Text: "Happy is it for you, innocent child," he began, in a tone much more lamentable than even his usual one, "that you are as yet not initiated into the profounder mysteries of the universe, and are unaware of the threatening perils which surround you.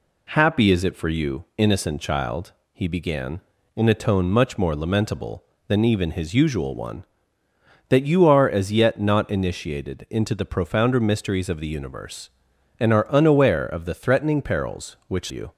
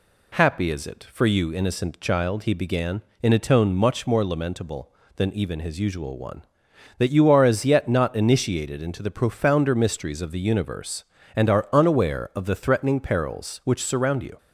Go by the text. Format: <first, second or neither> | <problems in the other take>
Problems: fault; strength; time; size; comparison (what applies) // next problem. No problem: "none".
second | skips "surround"; at 15.3 s